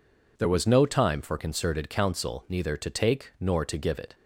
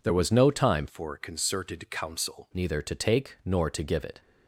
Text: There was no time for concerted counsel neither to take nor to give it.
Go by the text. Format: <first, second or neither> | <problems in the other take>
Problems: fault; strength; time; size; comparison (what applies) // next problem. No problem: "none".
first | changes voice from "for" to "counsel"; from 0.8 to 2.4 s; 1.6 s long